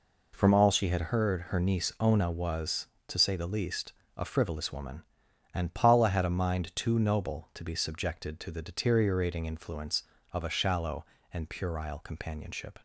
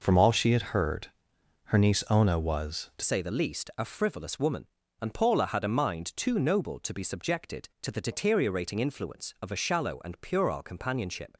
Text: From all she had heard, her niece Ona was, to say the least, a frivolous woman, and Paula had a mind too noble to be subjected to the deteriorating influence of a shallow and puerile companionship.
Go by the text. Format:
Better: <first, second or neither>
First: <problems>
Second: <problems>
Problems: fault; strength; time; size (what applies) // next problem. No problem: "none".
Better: first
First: none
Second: changes voice at "say"; from 3.0 s on; 8.3 s long